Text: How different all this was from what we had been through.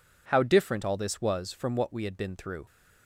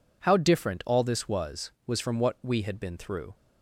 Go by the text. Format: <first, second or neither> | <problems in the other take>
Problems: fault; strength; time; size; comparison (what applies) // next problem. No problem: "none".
first | says "was" twice; at 1.8 s